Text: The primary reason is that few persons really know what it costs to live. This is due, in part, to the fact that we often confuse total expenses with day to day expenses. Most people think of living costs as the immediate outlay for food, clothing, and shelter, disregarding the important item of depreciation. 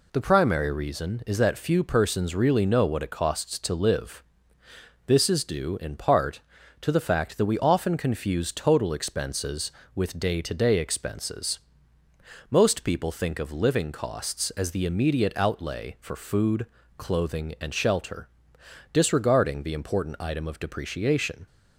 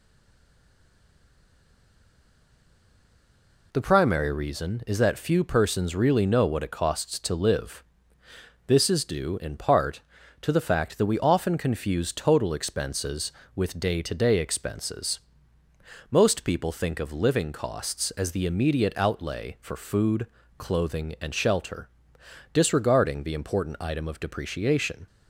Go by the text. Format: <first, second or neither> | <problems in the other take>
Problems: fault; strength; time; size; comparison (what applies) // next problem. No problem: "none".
first | stays silent before the first word; strong; until 3.7 s; 3.7 s long